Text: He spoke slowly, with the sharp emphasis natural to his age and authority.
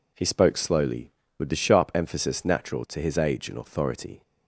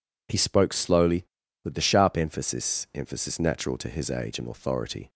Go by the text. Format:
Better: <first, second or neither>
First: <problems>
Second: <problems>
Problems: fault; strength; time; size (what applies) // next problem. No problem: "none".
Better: first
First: none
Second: says "emphasis" twice; at 2.9 s